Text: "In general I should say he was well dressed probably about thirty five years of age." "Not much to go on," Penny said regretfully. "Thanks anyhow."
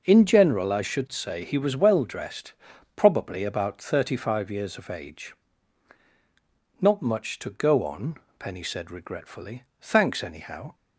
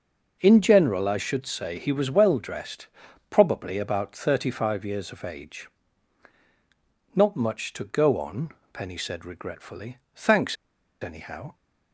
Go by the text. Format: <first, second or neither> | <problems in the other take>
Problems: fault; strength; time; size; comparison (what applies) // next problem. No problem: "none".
first | pauses between "dressed" and "probably"; at 2.8 s; 0.42 s long; also in the first // pauses between "Thanks" and "anyhow"; noticeable; at 10.5 s; 0.48 s long